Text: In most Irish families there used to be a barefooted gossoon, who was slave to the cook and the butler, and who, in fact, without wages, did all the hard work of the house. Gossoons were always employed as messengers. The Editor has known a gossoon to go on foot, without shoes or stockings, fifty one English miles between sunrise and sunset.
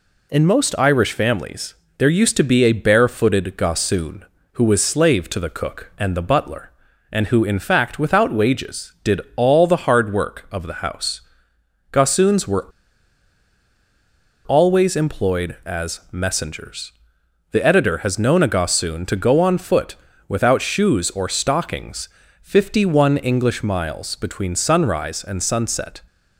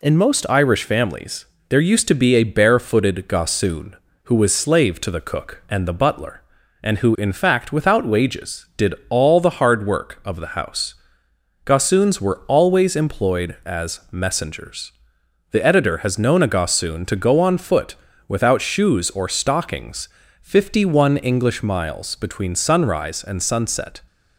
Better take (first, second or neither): second